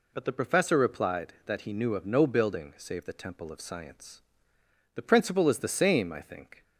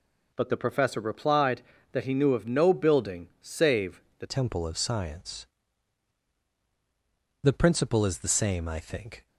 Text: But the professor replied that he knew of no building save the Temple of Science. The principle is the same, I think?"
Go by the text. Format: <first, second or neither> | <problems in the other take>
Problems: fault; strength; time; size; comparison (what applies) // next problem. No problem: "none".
first | pauses between "save" and "the"; slight; at 4.0 s; 0.18 s long // changes voice at "Temple"; from 4.2 s on; 5.0 s long